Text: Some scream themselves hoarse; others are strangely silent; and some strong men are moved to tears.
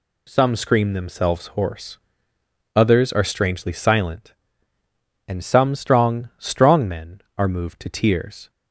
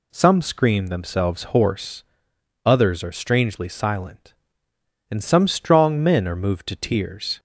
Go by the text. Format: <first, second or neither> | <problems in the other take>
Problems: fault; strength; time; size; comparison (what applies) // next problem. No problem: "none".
second | says "strong" twice; at 6.3 s